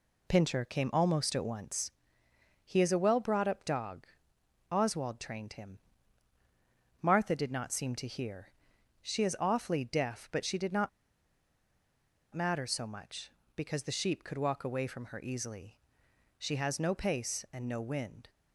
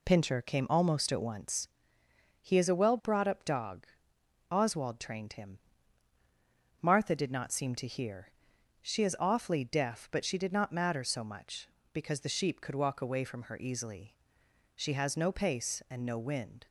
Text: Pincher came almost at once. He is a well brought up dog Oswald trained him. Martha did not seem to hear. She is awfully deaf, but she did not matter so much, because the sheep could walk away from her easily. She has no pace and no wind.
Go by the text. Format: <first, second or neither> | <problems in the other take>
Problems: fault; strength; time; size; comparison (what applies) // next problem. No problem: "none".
second | pauses between "dog" and "Oswald"; noticeable; at 4.0 s; 0.64 s long; noticeable in the second // pauses between "not" and "matter"; strong; at 10.8 s; 1.4 s long